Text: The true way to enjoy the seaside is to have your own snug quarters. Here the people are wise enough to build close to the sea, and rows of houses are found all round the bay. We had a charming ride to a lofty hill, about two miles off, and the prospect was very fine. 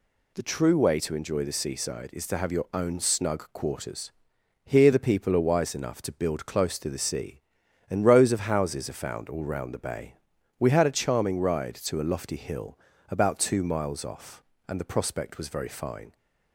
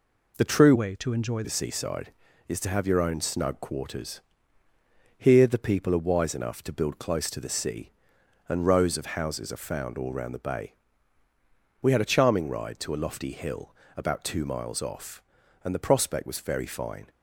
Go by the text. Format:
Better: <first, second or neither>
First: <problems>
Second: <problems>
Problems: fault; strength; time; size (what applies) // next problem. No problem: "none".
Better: first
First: none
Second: changes voice from "way" to "enjoy"; from 0.7 to 1.4 s; 0.7 s long